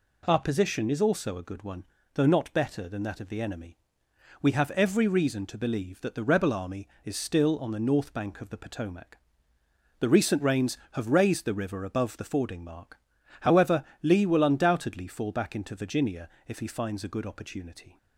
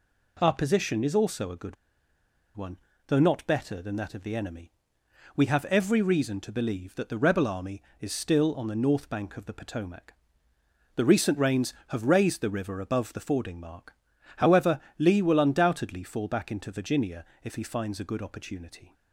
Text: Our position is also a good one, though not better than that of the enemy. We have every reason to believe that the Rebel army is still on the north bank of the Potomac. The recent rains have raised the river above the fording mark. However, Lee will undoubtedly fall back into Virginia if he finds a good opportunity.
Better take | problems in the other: first | pauses between "good" and "one"; noticeable; at 1.7 s; 0.81 s long // pauses between "Virginia" and "if"; slight; at 17.2 s; 0.18 s long; slight in the first

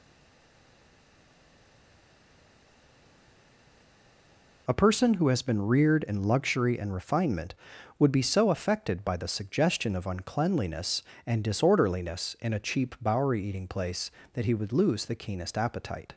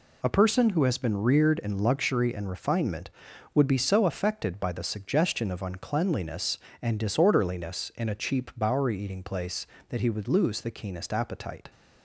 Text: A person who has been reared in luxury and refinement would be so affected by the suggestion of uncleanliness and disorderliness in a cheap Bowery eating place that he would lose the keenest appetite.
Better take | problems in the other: second | stays silent before the first word; strong; until 4.6 s; 4.6 s long

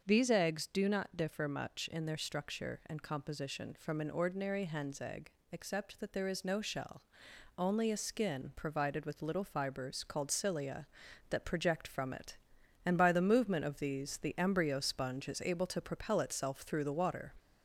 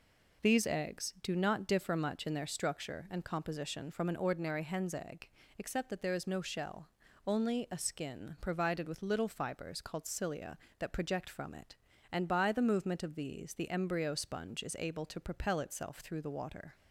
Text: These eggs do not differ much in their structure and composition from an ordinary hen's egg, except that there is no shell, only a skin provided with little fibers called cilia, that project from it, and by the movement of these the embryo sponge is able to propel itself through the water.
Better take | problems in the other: second | gets louder; slight; throughout; 2.5 dB // starts louder than the rest; until 1.0 s; 6 dB

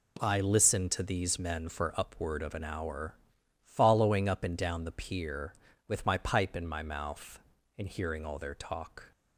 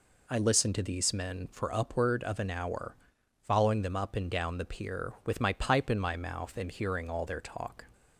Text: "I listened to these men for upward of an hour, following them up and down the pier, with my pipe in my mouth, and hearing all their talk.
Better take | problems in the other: second | skips "them"; at 4.2 s

